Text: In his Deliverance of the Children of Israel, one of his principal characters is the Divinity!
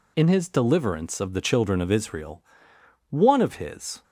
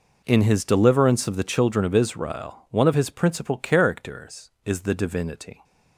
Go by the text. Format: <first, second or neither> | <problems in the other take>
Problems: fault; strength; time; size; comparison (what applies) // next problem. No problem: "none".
second | stops before "principal characters is the Divinity"; at 4.0 s